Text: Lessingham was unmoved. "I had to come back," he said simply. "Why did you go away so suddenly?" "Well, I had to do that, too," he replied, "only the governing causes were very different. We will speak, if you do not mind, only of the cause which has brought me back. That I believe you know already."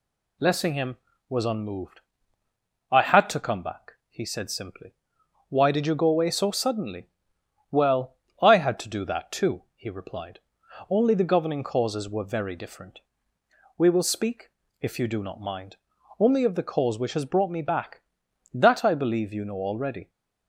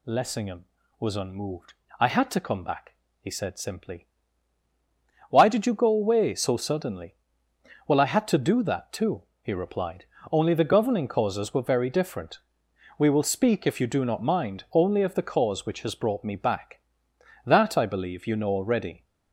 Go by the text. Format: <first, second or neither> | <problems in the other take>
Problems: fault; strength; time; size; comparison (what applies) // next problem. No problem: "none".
neither | none